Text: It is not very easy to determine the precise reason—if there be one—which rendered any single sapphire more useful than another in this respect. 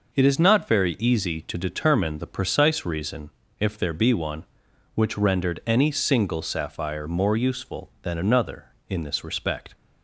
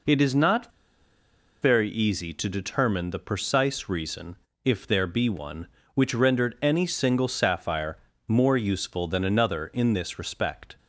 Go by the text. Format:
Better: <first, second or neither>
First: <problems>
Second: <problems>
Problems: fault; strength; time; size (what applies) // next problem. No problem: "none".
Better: first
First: none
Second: pauses between "not" and "very"; noticeable; at 0.6 s; 0.92 s long // pauses between "sapphire" and "more"; slight; at 7.9 s; 0.30 s long